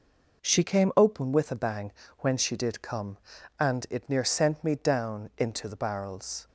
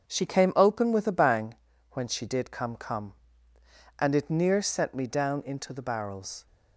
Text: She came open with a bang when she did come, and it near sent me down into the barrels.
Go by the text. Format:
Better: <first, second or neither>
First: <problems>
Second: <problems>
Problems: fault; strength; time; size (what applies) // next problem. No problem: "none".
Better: first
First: pauses between "bang" and "when"; slight; at 1.9 s; 0.28 s long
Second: starts louder than the rest; until 1.1 s; 7 dB // pauses between "bang" and "when"; slight; at 1.5 s; 0.36 s long // says "come" twice; at 2.7 s